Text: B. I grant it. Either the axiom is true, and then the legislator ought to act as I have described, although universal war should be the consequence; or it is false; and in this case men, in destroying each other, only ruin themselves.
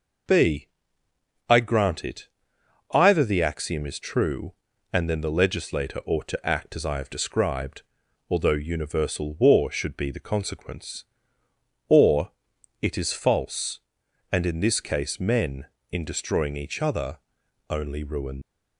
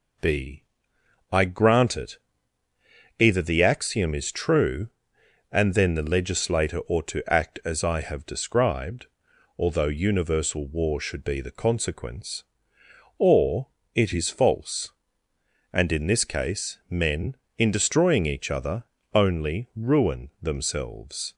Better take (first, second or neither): second